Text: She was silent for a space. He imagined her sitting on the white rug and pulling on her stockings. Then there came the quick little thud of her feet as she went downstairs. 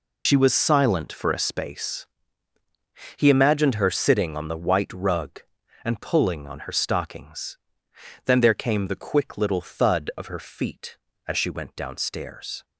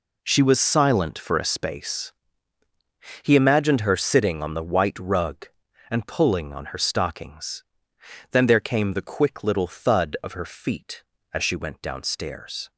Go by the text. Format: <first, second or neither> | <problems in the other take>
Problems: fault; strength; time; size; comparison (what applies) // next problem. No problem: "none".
second | loses the start of "She"; at 0.2 s; 90 ms